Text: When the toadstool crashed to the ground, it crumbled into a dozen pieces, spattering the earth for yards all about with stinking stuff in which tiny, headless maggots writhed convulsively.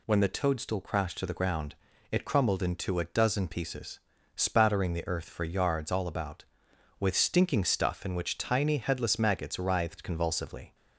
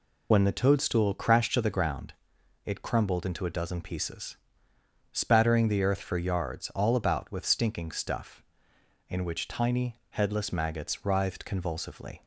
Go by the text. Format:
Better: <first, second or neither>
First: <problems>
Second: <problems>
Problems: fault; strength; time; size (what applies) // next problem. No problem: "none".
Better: first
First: none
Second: loses the start of "When"; at 0.3 s; 45 ms